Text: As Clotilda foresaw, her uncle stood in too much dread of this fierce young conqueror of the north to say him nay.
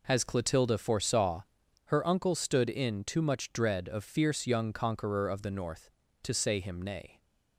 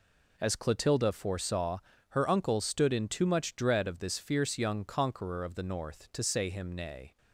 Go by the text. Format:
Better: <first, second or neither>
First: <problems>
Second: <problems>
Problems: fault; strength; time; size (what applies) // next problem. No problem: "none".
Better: second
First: skips "this"; at 4.0 s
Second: none